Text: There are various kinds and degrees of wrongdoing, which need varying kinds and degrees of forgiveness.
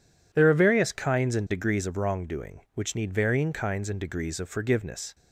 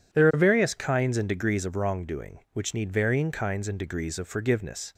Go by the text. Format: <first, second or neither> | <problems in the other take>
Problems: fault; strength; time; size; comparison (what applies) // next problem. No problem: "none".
neither | none